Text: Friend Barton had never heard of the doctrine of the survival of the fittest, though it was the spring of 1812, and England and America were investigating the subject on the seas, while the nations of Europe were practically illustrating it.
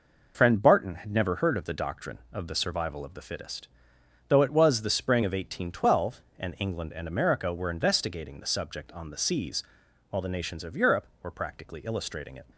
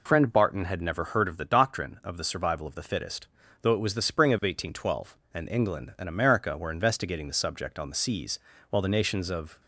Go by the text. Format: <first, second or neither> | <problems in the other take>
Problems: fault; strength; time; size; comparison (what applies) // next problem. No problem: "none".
first | stops before "Europe were practically illustrating it"; at 9.5 s